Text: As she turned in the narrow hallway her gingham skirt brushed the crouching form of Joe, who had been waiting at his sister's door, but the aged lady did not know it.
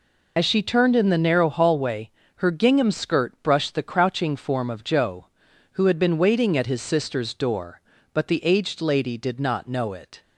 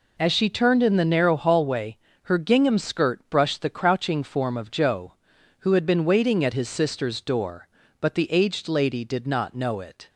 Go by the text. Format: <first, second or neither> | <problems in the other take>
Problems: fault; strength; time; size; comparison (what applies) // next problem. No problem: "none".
second | loses the start of "As"; at 0.3 s; 45 ms // pauses between "hallway" and "her"; slight; at 2.0 s; 0.26 s long; slight in the second